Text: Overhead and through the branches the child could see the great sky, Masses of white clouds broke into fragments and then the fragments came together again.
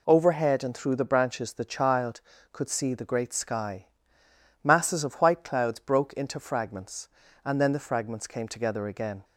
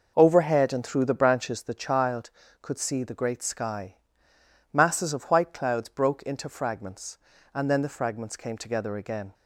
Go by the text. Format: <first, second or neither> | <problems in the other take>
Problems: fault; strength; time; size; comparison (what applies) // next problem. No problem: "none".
first | starts louder than the rest; noticeable; until 1.6 s; 5.5 dB